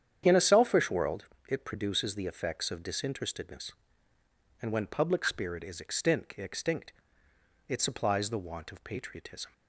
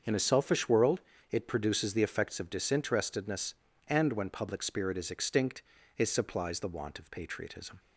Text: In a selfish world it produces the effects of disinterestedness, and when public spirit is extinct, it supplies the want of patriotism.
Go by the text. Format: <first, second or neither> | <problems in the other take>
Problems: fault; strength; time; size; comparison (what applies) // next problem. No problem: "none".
second | starts louder than the rest; strong; until 1.2 s; 9 dB; also in the second // pauses between "world" and "it"; slight; at 1.2 s; 0.22 s long; slight in the second // says "extinct" twice; at 6.3 s